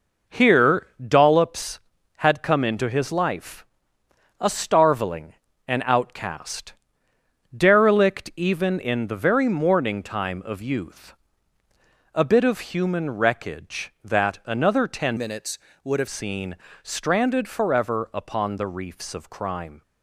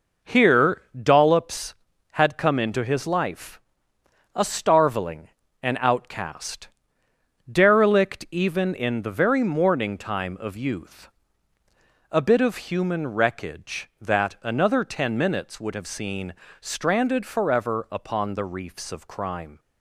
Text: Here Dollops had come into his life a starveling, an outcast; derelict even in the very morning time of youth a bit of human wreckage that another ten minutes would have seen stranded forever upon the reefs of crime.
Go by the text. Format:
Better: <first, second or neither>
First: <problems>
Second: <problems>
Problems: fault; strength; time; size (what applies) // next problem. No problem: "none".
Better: second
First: pauses between "Here" and "Dollops"; slight; at 0.8 s; 0.18 s long // pauses between "life" and "a"; noticeable; at 3.6 s; 0.76 s long // pauses between "youth" and "a"; at 11.1 s; 1.0 s long // changes voice from "minutes" to "have"; from 15.1 to 16.0 s; 0.9 s long // pauses between "seen" and "stranded"; slight; at 16.5 s; 0.26 s long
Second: pauses between "Here" and "Dollops"; slight; at 0.8 s; 0.18 s long // pauses between "life" and "a"; noticeable; at 3.5 s; 0.76 s long // pauses between "youth" and "a"; at 11.0 s; 1.0 s long // pauses between "seen" and "stranded"; slight; at 16.3 s; 0.26 s long